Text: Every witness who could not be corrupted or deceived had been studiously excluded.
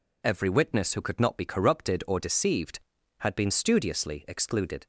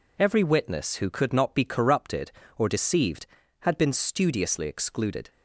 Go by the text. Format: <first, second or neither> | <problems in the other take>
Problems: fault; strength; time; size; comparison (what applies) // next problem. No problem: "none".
neither | none